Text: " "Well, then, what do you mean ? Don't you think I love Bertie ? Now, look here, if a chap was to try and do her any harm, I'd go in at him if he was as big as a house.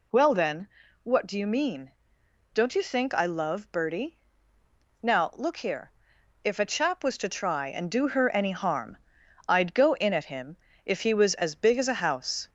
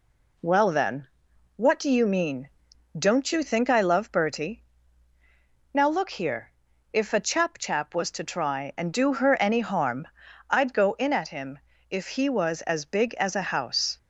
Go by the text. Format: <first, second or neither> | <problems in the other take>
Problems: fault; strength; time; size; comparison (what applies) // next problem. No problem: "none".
first | says "chap" twice; at 7.5 s // pauses between "him" and "if"; slight; at 11.5 s; 0.32 s long; slight in the first